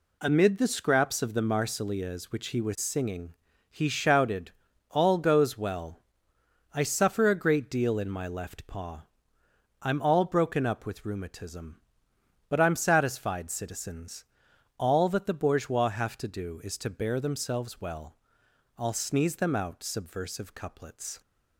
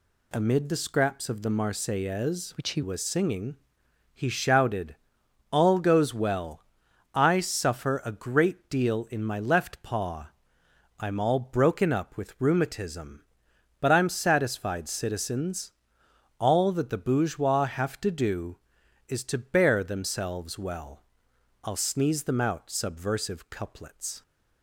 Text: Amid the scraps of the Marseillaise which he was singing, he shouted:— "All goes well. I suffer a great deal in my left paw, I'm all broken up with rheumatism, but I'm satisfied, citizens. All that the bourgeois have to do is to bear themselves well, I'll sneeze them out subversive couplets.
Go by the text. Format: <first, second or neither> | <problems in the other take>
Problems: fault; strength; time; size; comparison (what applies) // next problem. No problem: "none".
first | changes voice from "which" to "he"; from 2.5 to 2.8 s; 0.3 s long